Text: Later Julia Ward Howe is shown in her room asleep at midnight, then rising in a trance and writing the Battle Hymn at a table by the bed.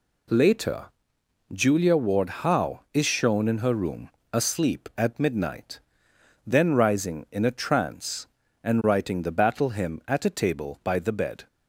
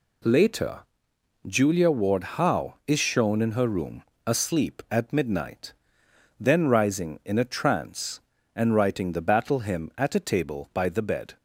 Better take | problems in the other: neither | pauses between "Later" and "Julia"; noticeable; the same in both // pauses between "room" and "asleep"; slight; the same in both

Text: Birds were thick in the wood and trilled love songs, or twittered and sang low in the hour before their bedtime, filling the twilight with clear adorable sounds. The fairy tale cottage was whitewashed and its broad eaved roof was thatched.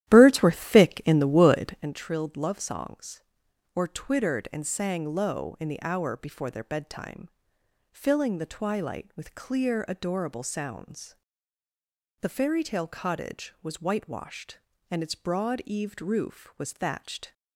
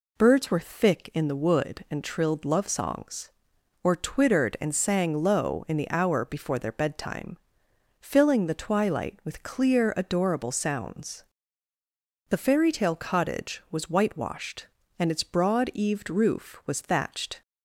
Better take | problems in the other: second | starts louder than the rest; strong; until 2.0 s; 13 dB

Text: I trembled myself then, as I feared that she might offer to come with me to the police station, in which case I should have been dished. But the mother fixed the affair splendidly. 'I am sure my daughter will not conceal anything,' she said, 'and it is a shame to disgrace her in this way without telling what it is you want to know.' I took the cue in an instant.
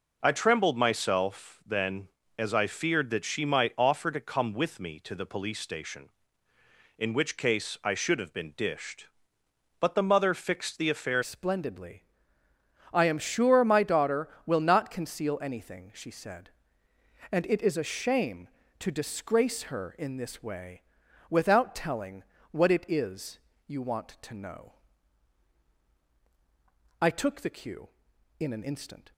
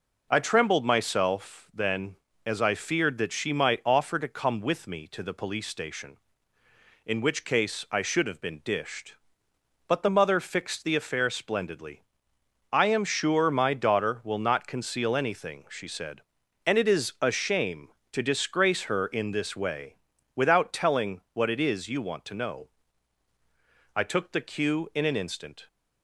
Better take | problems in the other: second | changes voice at "splendidly"; from 11.2 s on; 17.9 s long // pauses between "way" and "without"; noticeable; at 20.8 s; 0.48 s long; also in the second // pauses between "telling" and "what"; slight; at 22.2 s; 0.26 s long // pauses between "is" and "you"; slight; at 23.3 s; 0.30 s long

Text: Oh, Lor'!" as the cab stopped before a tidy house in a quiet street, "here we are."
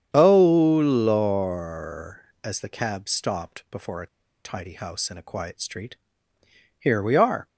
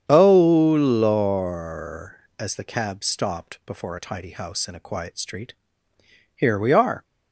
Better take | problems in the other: second | starts louder than the rest; strong; until 1.1 s; 8 dB; strong in the second // pauses between "a" and "tidy"; at 4.0 s; 0.38 s long

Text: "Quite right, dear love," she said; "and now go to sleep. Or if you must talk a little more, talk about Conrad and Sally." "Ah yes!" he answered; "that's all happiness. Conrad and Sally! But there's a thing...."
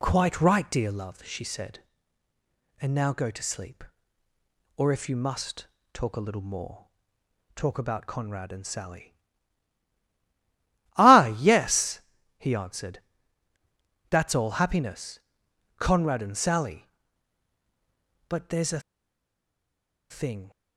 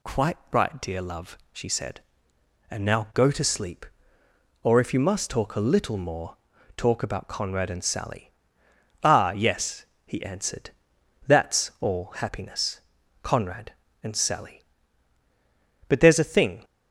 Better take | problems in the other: second | pauses between "must" and "talk"; slight; at 5.6 s; 0.26 s long // pauses between "a" and "thing"; strong; at 18.7 s; 1.3 s long

